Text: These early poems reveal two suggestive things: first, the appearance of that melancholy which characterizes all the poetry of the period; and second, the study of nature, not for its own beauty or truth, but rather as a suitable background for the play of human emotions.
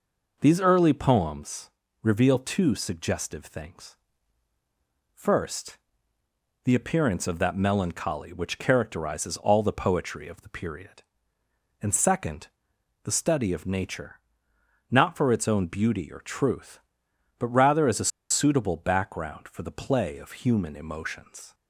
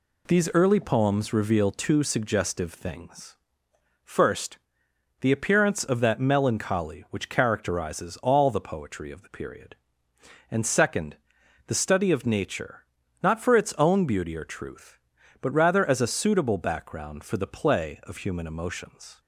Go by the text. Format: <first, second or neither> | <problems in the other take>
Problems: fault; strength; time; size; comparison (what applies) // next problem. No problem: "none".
second | pauses between "poems" and "reveal"; slight; at 1.6 s; 0.34 s long // pauses between "a" and "suitable"; slight; at 18.1 s; 0.21 s long